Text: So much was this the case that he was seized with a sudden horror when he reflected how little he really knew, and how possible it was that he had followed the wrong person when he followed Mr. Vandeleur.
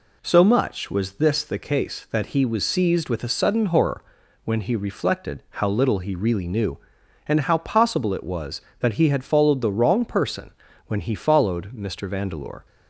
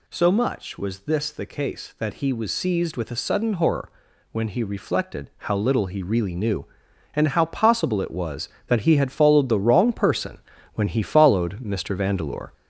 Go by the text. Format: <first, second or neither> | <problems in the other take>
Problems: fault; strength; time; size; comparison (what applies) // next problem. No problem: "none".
first | gets louder; noticeable; throughout; 5 dB // pauses between "horror" and "when"; at 3.9 s; 0.40 s long; also in the first // pauses between "person" and "when"; slight; at 10.3 s; 0.36 s long; slight in the first